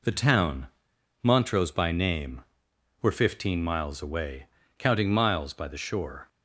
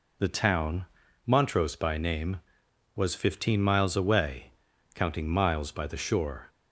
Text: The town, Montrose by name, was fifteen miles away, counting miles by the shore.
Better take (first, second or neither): second